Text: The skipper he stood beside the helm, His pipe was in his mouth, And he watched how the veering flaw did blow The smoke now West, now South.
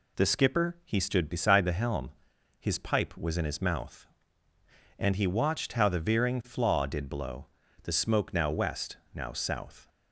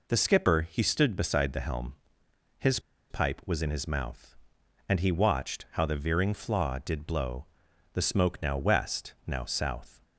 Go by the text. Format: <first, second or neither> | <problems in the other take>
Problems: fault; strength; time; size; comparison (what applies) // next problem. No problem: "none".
first | pauses between "His" and "pipe"; slight; at 2.7 s; 0.31 s long // pauses between "blow" and "The"; noticeable; at 7.4 s; 0.48 s long; also in the first